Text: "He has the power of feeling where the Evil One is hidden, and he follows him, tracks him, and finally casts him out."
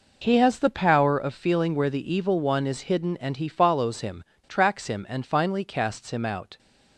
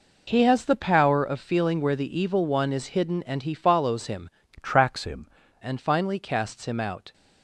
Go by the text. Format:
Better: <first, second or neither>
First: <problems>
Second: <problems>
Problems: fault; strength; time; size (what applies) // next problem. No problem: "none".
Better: first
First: none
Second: changes voice from "tracks" to "him"; from 4.6 to 5.2 s; 0.6 s long